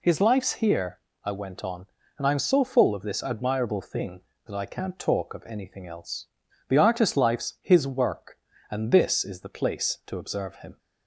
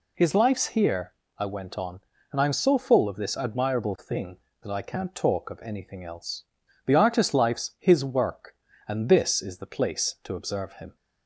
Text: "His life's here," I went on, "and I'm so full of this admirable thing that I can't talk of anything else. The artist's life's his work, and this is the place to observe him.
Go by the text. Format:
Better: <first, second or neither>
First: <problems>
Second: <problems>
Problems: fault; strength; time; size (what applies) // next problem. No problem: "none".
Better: neither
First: none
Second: none